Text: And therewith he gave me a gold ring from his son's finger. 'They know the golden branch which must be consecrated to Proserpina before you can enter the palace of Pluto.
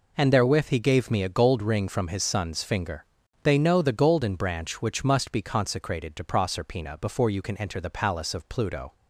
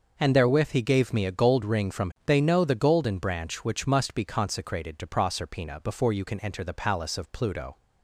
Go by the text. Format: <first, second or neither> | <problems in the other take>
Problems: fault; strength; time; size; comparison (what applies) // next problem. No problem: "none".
first | skips "his son's finger"; at 2.1 s